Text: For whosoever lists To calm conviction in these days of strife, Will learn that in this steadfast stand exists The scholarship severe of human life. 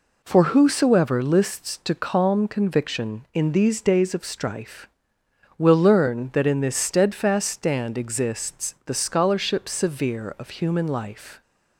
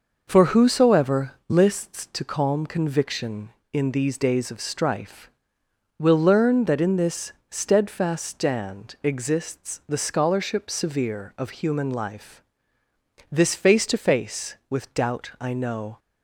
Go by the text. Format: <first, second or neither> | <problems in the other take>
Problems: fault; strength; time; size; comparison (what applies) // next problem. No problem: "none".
first | pauses between "whosoever" and "lists"; slight; at 1.3 s; 0.16 s long // pauses between "this" and "steadfast"; slight; at 7.3 s; 0.16 s long // goes on to say "This face to face with doubt I know"; strong; from 13.3 s on; 2.6 s long